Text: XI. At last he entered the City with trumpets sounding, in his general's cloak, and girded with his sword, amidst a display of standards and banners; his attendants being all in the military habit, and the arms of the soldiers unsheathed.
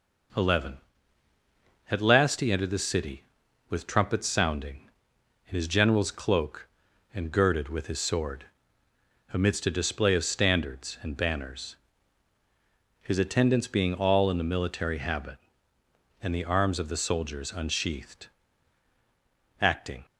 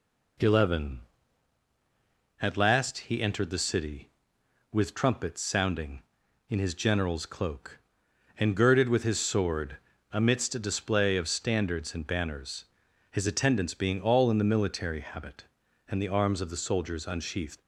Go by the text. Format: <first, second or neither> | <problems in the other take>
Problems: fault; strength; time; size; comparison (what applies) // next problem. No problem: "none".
second | goes on to say "Acting"; slight; from 19.5 s on; 0.46 s long